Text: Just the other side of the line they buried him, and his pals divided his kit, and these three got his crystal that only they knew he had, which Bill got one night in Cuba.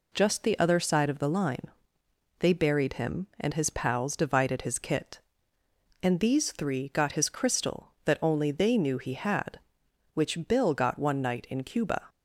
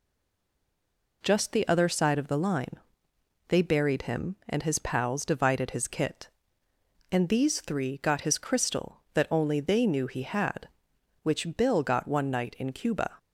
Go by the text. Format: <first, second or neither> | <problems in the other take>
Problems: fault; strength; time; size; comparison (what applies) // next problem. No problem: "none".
first | stays silent before the first word; noticeable; until 1.2 s; 1.2 s long // pauses between "line" and "they"; noticeable; at 2.7 s; 0.70 s long; noticeable in the first